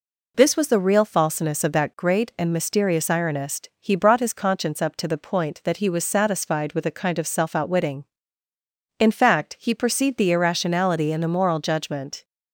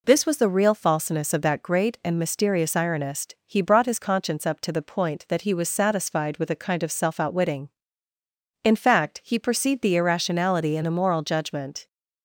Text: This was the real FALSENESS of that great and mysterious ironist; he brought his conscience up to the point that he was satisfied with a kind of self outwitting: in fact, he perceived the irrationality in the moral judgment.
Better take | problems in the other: neither | none

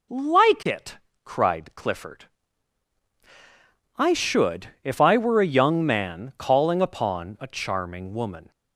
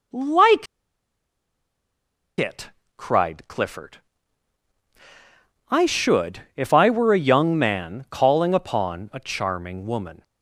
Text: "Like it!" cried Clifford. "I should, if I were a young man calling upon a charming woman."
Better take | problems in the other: first | pauses between "Like" and "it"; strong; at 0.6 s; 1.7 s long

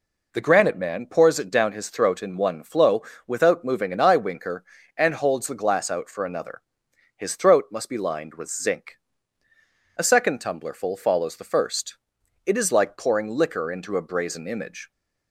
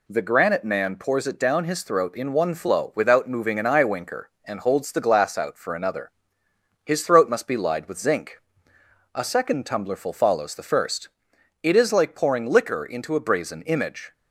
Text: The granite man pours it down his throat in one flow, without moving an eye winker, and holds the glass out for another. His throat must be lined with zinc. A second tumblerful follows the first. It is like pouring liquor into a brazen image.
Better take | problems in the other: first | says "lied" for "lined"; at 7.5 s

